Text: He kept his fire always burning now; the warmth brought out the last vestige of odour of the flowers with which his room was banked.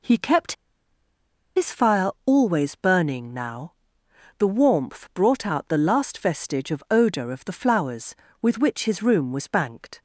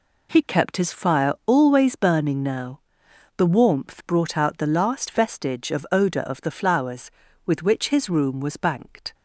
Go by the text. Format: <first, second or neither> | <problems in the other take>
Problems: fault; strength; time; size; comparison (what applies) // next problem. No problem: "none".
second | pauses between "kept" and "his"; at 0.5 s; 1.0 s long